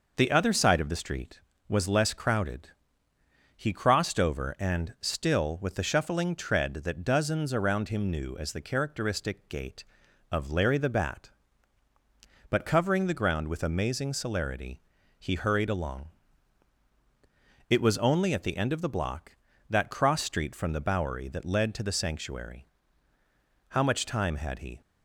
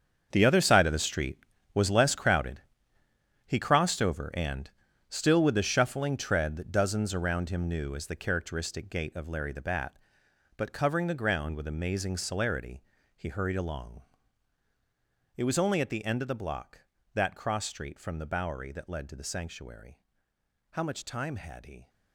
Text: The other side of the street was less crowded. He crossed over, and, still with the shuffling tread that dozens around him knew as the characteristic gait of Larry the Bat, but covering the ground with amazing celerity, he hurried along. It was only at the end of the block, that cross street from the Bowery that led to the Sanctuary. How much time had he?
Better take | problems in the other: first | gets quieter; strong; throughout; 13.5 dB

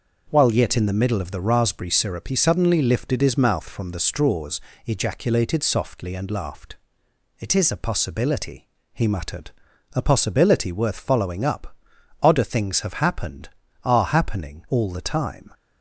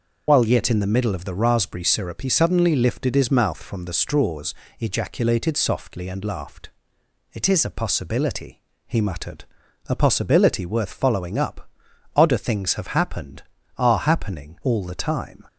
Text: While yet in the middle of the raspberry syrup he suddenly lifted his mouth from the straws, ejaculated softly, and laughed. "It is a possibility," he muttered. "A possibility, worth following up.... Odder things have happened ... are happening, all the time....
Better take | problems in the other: first | loses the start of "While"; at 0.2 s; 70 ms

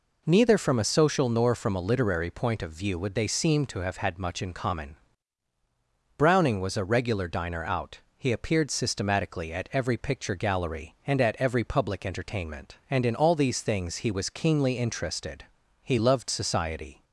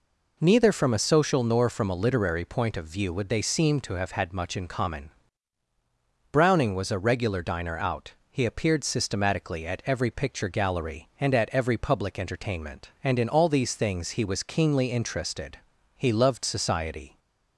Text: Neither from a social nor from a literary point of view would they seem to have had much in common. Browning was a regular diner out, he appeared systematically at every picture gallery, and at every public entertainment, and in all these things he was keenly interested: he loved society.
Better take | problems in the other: neither | none

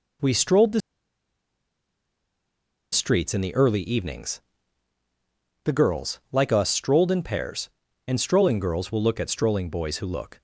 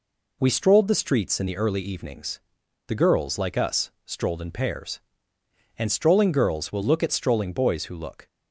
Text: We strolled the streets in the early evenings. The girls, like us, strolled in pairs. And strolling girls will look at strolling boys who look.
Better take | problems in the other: second | pauses between "the" and "streets"; strong; at 0.8 s; 2.1 s long

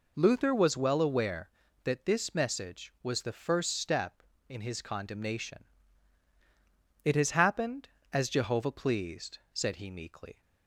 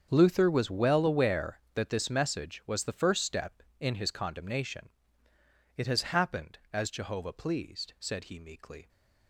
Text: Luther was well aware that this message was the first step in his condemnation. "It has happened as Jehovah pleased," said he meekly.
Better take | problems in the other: first | gets quieter; strong; throughout; 15.5 dB

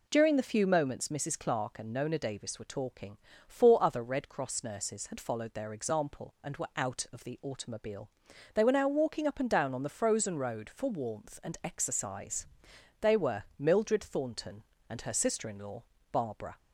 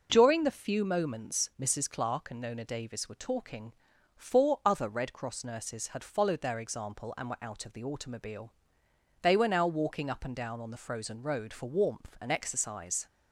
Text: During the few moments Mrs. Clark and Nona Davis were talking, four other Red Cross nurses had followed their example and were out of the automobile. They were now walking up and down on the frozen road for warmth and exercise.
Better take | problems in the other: second | goes on to say "They were Mildred Thornton and her sister in law Barbara"; strong; from 13.0 s on; 3.5 s long

